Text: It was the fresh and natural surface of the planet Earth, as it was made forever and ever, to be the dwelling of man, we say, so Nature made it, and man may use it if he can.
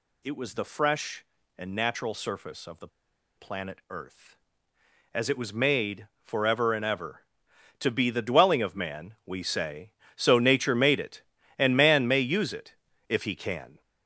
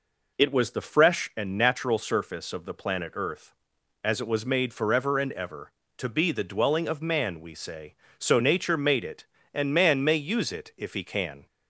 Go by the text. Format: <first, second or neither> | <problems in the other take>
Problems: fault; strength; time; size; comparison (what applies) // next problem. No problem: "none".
second | pauses between "the" and "planet"; noticeable; at 2.8 s; 0.49 s long // pauses between "made" and "forever"; slight; at 6.0 s; 0.16 s long // pauses between "it" and "if"; slight; at 12.7 s; 0.34 s long